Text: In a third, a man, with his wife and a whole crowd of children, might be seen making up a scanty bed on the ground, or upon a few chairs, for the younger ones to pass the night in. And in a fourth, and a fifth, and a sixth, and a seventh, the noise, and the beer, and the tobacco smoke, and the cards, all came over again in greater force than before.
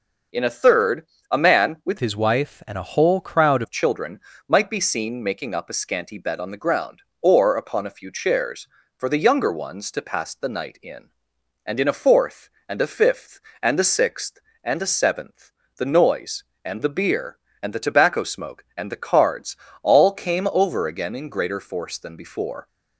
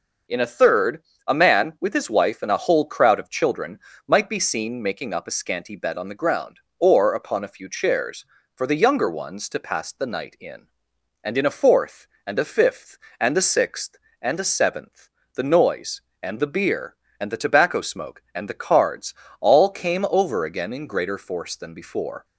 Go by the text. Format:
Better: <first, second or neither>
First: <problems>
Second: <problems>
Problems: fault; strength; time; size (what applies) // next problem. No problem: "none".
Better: second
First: changes voice from "his" to "crowd"; from 2.0 to 3.6 s; 1.6 s long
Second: none